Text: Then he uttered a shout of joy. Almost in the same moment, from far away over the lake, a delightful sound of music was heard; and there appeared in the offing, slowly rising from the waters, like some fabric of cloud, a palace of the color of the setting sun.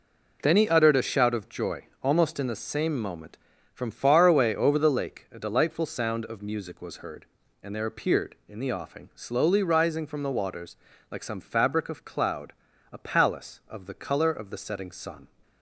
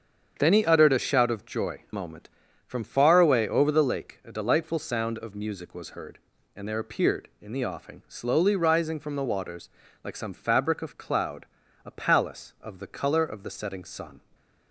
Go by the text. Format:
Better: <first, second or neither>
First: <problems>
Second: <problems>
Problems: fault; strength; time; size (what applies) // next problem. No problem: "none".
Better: first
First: none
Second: starts louder than the rest; strong; until 1.4 s; 7.5 dB // skips "Almost in the same"; at 1.8 s